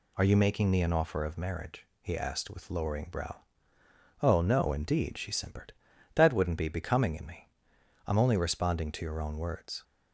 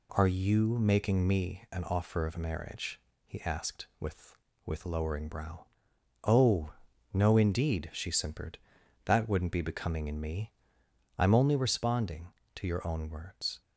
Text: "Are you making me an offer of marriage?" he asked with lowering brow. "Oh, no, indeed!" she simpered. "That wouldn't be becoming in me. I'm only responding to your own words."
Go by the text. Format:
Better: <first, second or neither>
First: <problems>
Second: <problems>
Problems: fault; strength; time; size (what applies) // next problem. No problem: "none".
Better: first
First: none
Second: says "with" twice; at 4.6 s